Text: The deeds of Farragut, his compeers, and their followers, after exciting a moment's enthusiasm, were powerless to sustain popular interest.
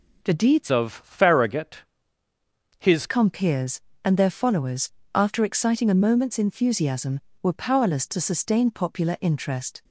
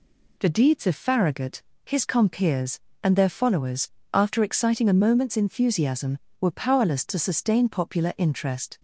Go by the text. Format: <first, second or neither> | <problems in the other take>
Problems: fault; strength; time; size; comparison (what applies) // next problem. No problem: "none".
second | changes voice from "of" to "his"; from 0.7 to 3.0 s; 2.3 s long